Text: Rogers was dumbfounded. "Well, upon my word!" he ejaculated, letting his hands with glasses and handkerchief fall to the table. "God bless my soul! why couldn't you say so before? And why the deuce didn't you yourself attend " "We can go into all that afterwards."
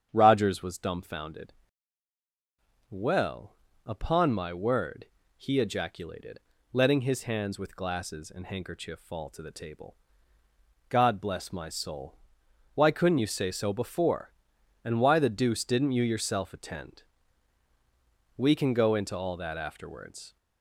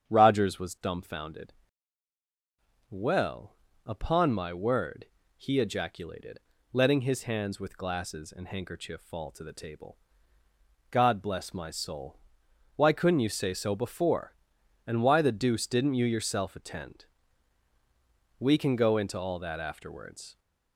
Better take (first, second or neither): neither